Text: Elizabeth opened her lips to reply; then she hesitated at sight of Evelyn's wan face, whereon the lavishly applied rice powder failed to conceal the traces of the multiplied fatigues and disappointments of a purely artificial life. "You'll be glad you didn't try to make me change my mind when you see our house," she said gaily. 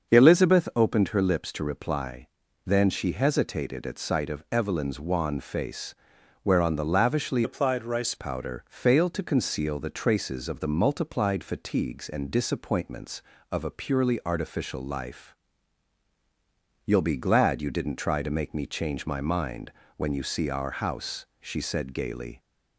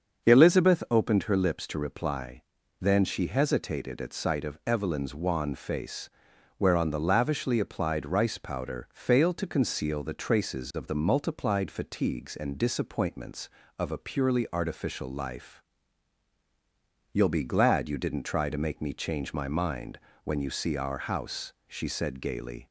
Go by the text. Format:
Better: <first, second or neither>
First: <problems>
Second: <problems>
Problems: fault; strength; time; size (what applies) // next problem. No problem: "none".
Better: second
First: starts louder than the rest; until 1.1 s; 6.5 dB // changes voice from "applied" to "rice"; from 7.4 to 8.1 s; 0.7 s long // pauses between "mind" and "when"; slight; at 19.6 s; 0.28 s long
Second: starts louder than the rest; until 1.2 s; 6.5 dB // pauses between "mind" and "when"; slight; at 19.9 s; 0.28 s long